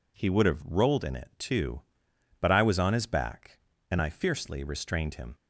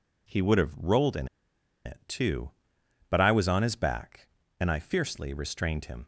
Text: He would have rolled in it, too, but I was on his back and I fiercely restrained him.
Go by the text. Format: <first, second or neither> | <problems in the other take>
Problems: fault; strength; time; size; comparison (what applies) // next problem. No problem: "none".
first | pauses between "in" and "it"; noticeable; at 1.2 s; 0.59 s long